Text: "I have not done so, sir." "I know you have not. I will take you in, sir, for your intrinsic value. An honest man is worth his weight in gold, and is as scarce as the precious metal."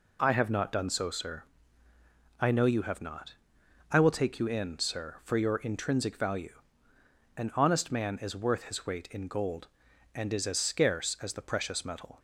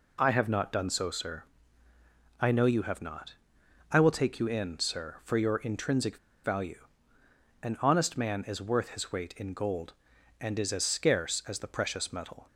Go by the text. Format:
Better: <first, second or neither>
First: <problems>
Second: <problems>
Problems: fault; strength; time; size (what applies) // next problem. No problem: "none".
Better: first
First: none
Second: pauses between "intrinsic" and "value"; slight; at 6.1 s; 0.27 s long